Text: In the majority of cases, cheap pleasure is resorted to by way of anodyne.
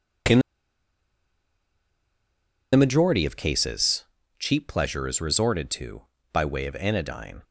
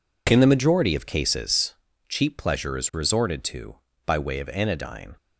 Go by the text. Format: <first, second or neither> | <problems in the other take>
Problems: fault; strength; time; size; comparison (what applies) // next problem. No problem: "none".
second | pauses between "In" and "the"; strong; at 0.3 s; 2.3 s long